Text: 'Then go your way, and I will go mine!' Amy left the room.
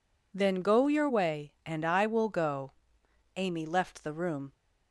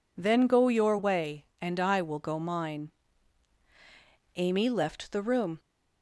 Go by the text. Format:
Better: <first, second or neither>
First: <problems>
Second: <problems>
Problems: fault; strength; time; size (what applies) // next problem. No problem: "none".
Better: second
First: skips "mine"; at 3.0 s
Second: none